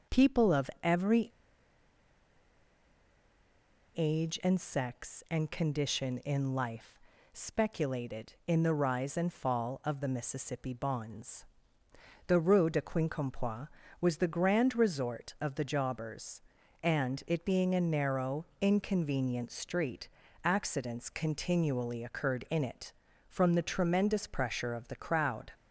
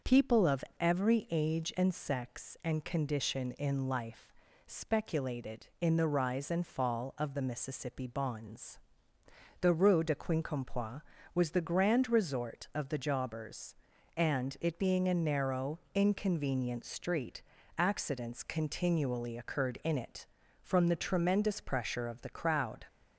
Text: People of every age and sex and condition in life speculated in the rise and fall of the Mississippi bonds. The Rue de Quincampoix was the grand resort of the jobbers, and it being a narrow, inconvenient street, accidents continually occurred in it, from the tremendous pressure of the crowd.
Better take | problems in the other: second | starts louder than the rest; until 1.2 s; 6 dB; also in the second // pauses between "every" and "age"; strong; at 1.3 s; 2.6 s long // pauses between "life" and "speculated"; slight; at 6.9 s; 0.36 s long; slight in the second

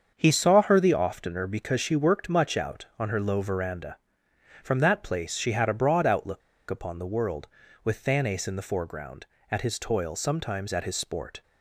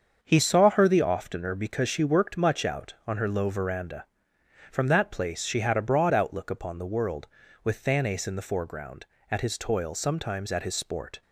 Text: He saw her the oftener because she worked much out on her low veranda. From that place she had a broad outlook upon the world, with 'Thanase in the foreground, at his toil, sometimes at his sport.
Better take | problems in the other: second | starts louder than the rest; until 1.1 s; 7 dB; also in the second // pauses between "outlook" and "upon"; slight; at 6.4 s; 0.29 s long

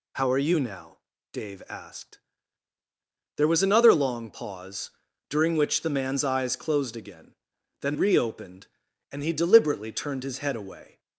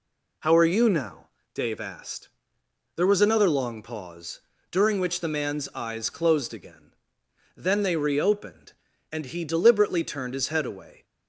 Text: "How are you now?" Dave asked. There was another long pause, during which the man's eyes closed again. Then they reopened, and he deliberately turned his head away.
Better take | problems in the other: second | skips "they"; at 7.9 s

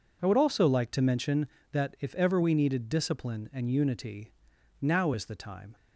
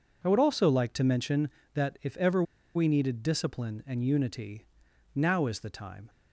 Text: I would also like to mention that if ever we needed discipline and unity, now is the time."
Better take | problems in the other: first | pauses between "ever" and "we"; slight; at 2.4 s; 0.31 s long

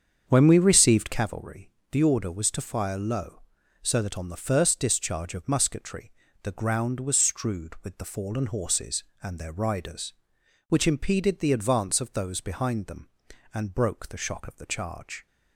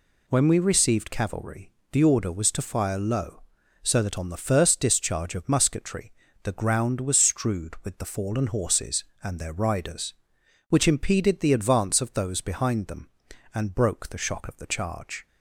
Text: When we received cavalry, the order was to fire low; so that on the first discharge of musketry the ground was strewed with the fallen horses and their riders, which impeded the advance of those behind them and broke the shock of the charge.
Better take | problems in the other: second | starts louder than the rest; strong; until 1.3 s; 7.5 dB // pauses between "musketry" and "the"; slight; at 6.1 s; 0.32 s long; slight in the second

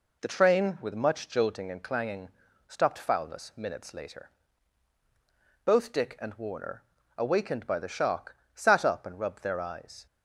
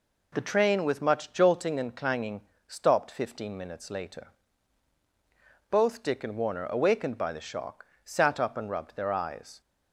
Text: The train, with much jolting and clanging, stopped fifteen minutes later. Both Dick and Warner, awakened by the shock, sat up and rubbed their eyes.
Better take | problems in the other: second | says "foulness" for "fifteen"; at 2.9 s

